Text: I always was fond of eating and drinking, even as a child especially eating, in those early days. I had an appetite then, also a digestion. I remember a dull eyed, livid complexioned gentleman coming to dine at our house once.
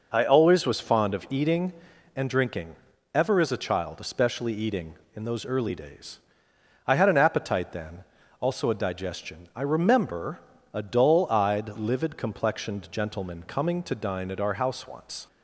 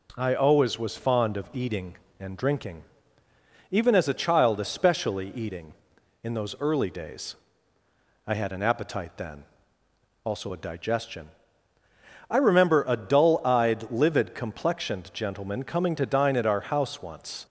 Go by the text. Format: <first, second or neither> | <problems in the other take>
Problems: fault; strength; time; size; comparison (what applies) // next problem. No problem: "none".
second | says "ever" for "even"; at 3.1 s // pauses between "remember" and "a"; slight; at 10.3 s; 0.36 s long